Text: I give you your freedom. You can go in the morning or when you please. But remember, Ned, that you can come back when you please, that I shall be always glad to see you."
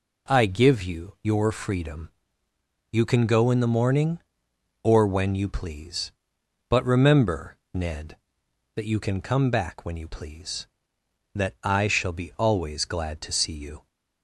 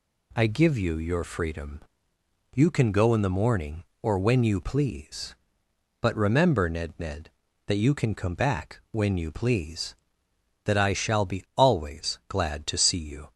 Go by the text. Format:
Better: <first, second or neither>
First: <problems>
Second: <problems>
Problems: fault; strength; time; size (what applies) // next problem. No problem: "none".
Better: first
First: none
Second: says "Ned" twice; at 6.9 s